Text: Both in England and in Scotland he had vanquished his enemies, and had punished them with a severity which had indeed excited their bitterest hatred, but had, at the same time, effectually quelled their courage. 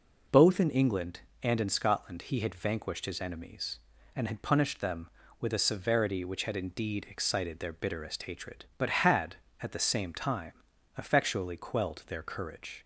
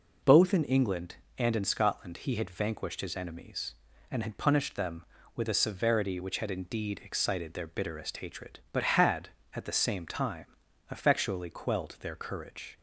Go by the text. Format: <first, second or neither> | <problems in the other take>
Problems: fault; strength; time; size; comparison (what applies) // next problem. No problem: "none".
neither | none